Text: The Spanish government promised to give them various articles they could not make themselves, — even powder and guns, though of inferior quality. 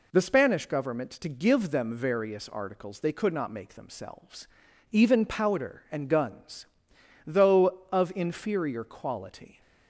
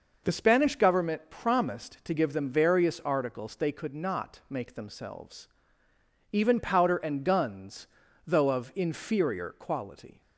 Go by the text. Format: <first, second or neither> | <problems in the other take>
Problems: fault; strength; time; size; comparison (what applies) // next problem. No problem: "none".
second | skips "promised"; at 1.1 s